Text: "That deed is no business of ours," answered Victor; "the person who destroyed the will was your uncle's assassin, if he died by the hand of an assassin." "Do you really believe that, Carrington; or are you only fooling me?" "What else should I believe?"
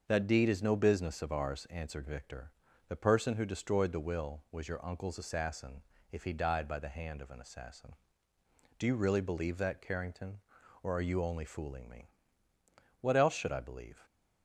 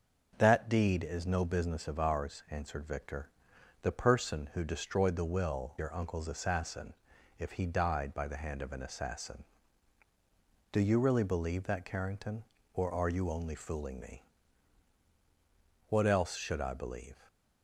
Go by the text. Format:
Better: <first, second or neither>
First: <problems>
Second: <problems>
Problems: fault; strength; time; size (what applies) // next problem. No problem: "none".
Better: first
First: starts louder than the rest; until 1.0 s; 6.5 dB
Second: starts louder than the rest; noticeable; until 1.3 s; 6 dB // skips "was"; at 5.7 s